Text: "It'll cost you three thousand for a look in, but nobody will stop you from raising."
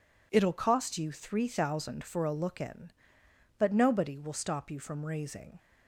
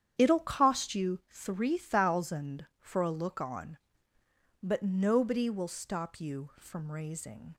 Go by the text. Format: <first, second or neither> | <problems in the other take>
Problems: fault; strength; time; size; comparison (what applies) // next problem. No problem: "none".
first | starts louder than the rest; strong; until 1.1 s; 9 dB // says "on" for "in"; at 3.3 s